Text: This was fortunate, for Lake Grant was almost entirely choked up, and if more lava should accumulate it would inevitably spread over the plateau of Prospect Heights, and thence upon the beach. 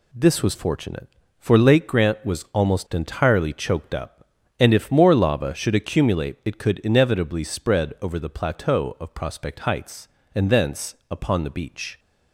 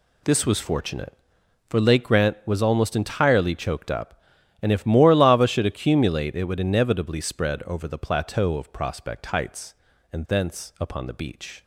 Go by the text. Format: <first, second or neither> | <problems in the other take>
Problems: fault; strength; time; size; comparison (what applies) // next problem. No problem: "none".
second | says "could" for "would"; at 6.5 s // pauses between "thence" and "upon"; slight; at 10.9 s; 0.16 s long